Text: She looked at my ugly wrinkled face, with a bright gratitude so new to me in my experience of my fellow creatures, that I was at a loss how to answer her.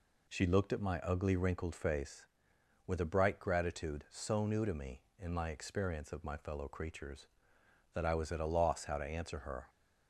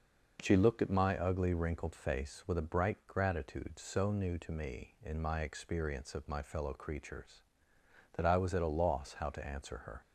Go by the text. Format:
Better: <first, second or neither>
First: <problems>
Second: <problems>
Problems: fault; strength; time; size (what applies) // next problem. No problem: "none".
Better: neither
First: none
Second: none